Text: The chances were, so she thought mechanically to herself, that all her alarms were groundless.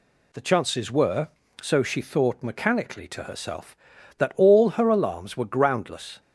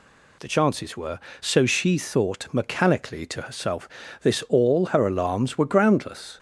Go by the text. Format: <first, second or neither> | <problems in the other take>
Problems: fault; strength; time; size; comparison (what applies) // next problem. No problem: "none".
first | says "this" for "that"; at 4.2 s